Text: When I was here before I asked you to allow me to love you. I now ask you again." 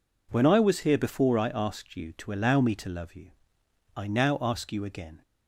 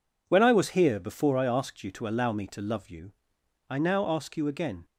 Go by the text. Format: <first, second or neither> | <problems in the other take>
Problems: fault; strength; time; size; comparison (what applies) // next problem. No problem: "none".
neither | none